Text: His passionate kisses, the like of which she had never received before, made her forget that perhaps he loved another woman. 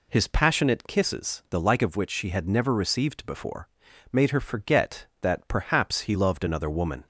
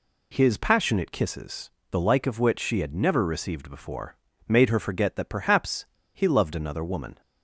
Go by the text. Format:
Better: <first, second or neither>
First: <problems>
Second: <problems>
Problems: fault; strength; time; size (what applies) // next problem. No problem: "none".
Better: first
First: none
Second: pauses between "perhaps" and "he"; slight; at 5.8 s; 0.29 s long